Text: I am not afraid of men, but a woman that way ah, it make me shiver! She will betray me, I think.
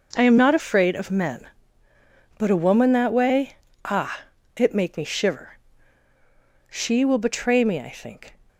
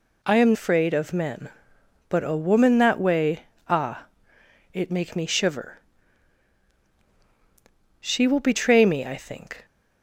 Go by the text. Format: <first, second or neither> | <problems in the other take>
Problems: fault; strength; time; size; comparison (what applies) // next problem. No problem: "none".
first | skips "not"; at 0.5 s // pauses between "way" and "ah"; slight; at 3.4 s; 0.22 s long; slight in the first